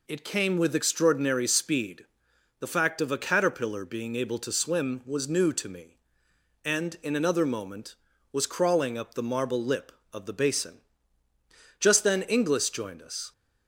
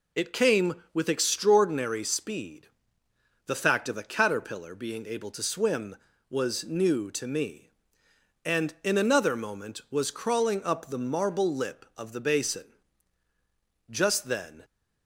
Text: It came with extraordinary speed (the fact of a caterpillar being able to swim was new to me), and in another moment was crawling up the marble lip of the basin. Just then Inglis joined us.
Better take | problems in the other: first | stops before "Inglis joined us"; at 14.6 s

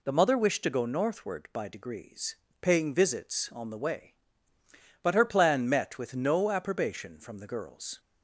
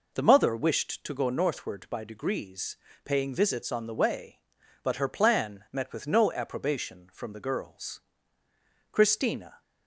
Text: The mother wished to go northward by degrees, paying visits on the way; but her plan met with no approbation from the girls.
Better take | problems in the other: first | goes on to say "Christina"; noticeable; from 8.9 s on; 0.70 s long

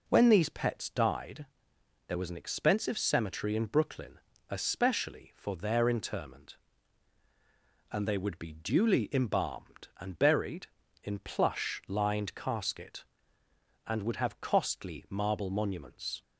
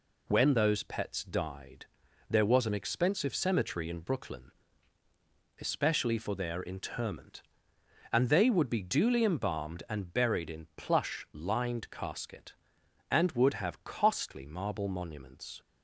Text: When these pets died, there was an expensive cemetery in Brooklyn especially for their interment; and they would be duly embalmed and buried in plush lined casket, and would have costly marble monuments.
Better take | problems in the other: first | says "those" for "these"; at 0.5 s // pauses between "Brooklyn" and "especially"; at 4.5 s; 1.0 s long; slight in the first

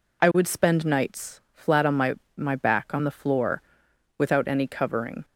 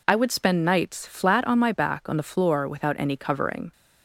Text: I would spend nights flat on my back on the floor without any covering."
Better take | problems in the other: second | says "my" twice; at 2.3 s // pauses between "floor" and "without"; noticeable; at 3.6 s; 0.54 s long

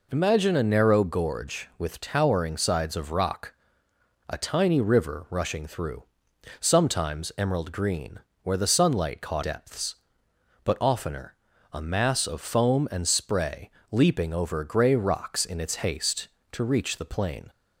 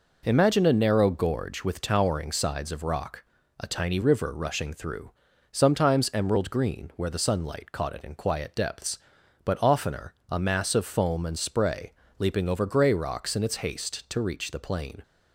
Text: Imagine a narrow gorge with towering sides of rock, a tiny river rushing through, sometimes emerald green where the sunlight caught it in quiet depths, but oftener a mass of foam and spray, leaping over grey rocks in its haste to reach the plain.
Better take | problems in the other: second | pauses between "green" and "where"; slight; at 8.1 s; 0.24 s long // skips "it in quiet"; at 9.4 s // pauses between "oftener" and "a"; at 11.3 s; 0.38 s long; slight in the second

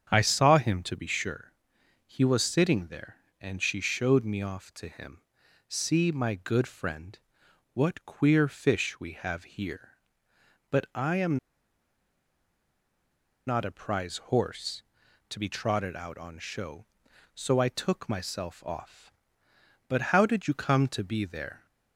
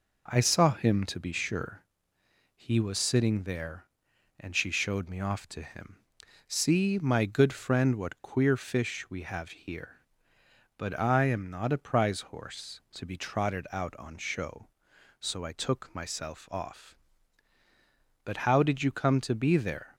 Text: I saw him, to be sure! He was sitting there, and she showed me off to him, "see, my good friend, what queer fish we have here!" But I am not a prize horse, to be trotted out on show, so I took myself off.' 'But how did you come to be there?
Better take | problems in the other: second | starts louder than the rest; strong; until 1.1 s; 8 dB // pauses between "am" and "not"; strong; at 11.3 s; 2.1 s long // pauses between "prize" and "horse"; slight; at 14.1 s; 0.16 s long

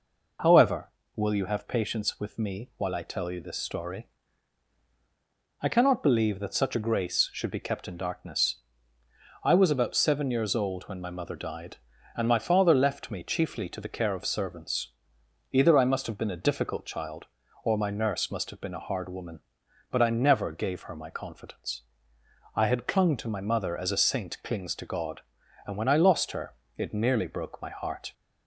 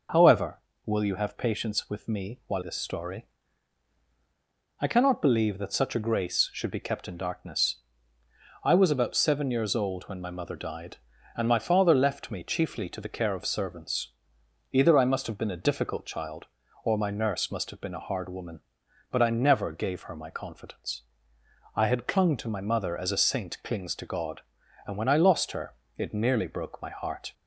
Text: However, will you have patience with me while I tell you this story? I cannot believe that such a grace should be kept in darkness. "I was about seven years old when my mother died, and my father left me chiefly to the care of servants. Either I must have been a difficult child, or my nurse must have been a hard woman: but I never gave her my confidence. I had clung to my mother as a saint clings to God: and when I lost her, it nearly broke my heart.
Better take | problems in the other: first | skips "I tell you"; at 2.6 s

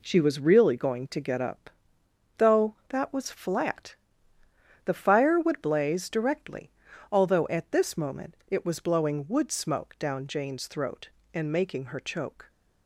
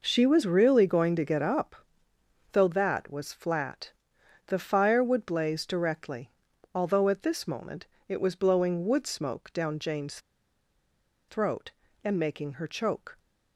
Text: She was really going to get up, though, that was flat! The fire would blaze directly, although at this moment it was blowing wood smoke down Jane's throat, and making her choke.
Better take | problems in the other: first | pauses between "moment" and "it"; slight; at 7.8 s; 0.22 s long // pauses between "Jane's" and "throat"; at 10.1 s; 1.0 s long

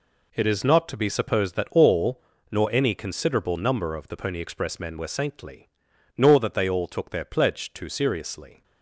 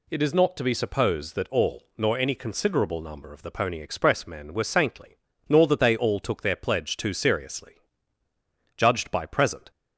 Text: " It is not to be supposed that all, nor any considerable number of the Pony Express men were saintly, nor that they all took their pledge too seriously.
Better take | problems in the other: first | goes on to say "Judged by present"; noticeable; from 8.7 s on; 0.96 s long

